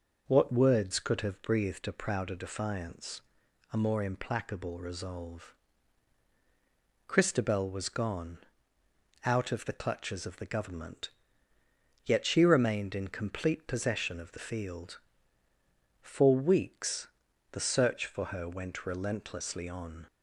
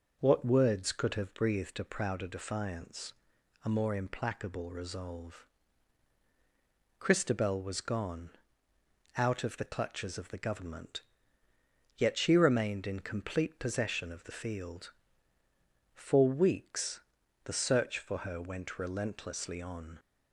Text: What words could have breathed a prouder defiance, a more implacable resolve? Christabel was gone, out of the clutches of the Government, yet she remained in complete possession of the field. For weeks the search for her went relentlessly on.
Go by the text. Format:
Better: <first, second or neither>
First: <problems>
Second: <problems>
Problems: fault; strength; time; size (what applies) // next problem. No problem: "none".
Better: neither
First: pauses between "weeks" and "the"; at 17.0 s; 0.42 s long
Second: pauses between "weeks" and "the"; at 17.0 s; 0.42 s long